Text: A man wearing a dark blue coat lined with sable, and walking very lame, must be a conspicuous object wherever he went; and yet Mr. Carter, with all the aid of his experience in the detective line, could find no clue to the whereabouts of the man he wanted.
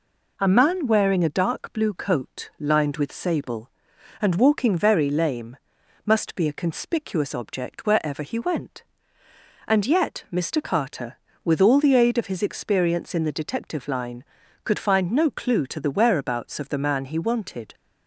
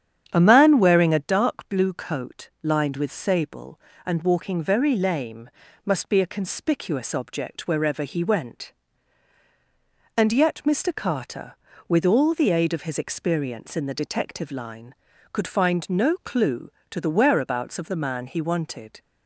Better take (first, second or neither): first